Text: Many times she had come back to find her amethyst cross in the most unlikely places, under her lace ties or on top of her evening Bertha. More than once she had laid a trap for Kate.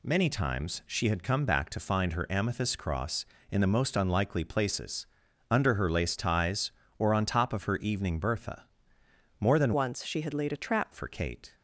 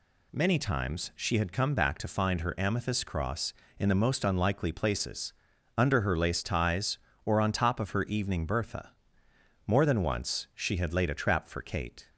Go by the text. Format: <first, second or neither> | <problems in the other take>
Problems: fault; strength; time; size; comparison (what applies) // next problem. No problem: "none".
second | changes voice from "once" to "trap"; from 9.7 to 10.9 s; 1.2 s long